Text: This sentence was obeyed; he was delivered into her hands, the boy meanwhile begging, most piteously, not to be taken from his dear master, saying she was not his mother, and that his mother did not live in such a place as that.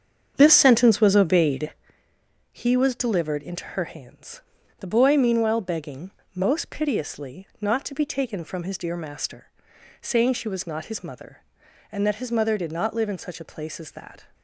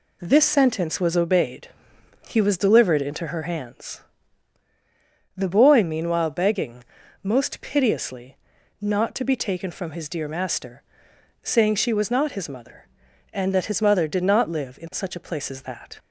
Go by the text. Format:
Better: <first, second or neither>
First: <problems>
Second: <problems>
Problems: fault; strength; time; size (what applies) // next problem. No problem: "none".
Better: second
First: starts louder than the rest; strong; until 1.9 s; 7.5 dB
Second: none